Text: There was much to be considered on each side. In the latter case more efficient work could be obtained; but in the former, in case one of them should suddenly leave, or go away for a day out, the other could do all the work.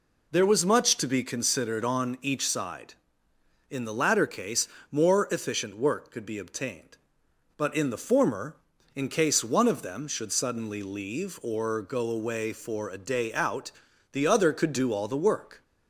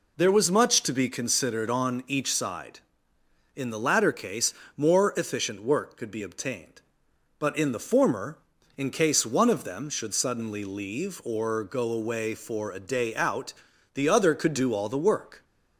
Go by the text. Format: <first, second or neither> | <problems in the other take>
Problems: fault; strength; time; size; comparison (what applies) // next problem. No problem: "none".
neither | pauses between "case" and "more"; slight; the same in both